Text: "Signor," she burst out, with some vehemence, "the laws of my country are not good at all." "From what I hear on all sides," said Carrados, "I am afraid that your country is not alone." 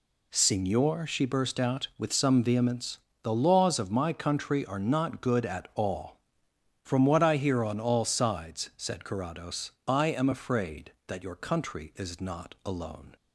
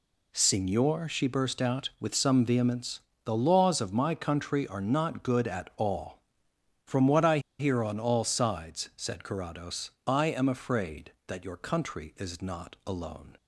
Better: first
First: none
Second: pauses between "I" and "hear"; slight; at 7.3 s; 0.20 s long

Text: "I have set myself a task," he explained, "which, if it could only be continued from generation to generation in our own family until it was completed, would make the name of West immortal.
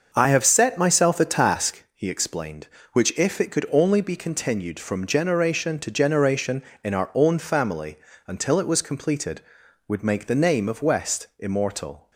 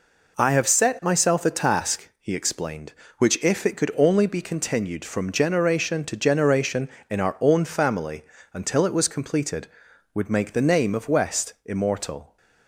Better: second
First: starts louder than the rest; until 1.8 s; 6.5 dB // pauses between "family" and "until"; slight; at 7.9 s; 0.30 s long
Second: pauses between "family" and "until"; slight; at 8.2 s; 0.30 s long

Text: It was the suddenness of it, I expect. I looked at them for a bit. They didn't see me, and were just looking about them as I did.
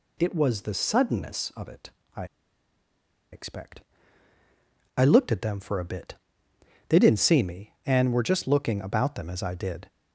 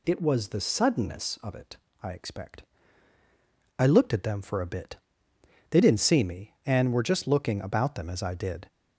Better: second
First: pauses between "I" and "expect"; at 2.2 s; 1.0 s long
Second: none

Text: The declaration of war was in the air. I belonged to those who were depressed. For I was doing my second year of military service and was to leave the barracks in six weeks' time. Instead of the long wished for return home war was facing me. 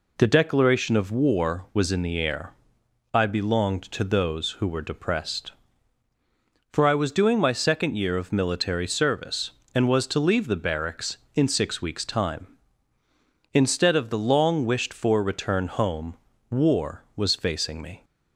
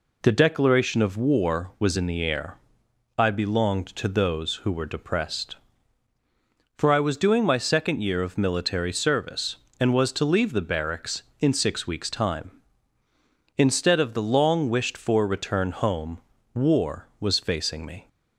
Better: neither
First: pauses between "home" and "war"; slight; at 16.1 s; 0.34 s long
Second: pauses between "home" and "war"; slight; at 16.1 s; 0.34 s long

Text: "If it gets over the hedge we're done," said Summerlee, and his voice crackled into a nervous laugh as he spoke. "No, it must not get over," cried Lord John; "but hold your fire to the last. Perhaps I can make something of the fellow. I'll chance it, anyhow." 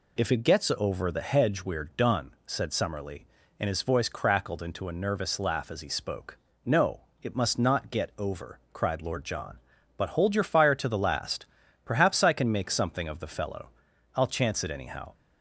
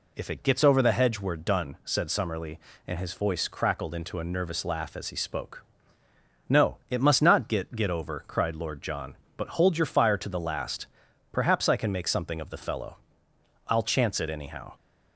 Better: first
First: none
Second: says "get" twice; at 7.7 s

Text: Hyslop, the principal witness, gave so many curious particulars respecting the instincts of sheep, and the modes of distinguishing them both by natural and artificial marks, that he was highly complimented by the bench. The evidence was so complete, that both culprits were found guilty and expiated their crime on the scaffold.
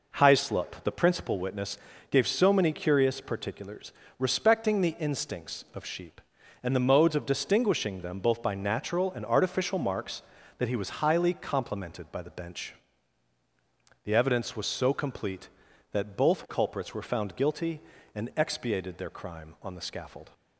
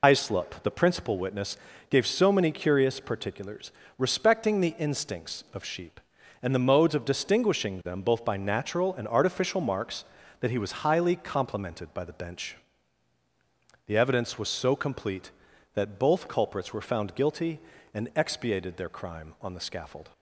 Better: first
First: pauses between "particulars" and "respecting"; slight; at 3.9 s; 0.26 s long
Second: loses the start of "Hyslop"; at 0.0 s; 105 ms // pauses between "particulars" and "respecting"; slight; at 3.7 s; 0.26 s long

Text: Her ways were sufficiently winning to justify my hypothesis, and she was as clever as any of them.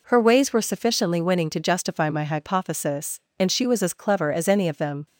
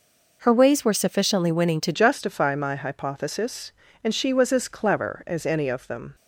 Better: first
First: none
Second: changes voice at "justify"; from 1.9 s on; 4.2 s long

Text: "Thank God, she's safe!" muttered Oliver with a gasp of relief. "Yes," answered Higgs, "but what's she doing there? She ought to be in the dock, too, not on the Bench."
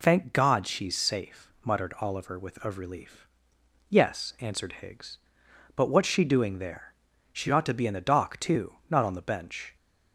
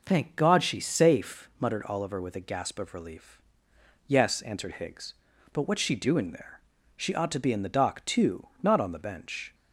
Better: second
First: skips "a gasp"; at 2.6 s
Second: none

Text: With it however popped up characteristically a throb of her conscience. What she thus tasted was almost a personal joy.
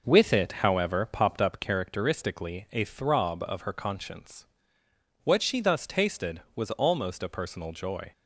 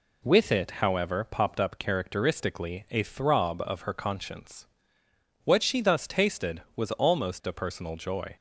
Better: second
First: starts louder than the rest; noticeable; until 1.9 s; 5.5 dB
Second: none

